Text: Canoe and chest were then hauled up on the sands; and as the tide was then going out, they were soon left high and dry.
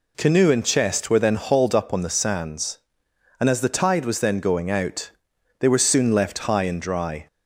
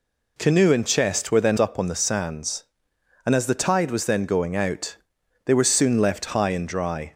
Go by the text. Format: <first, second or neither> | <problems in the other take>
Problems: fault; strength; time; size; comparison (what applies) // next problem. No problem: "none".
first | skips "hauled"; at 1.5 s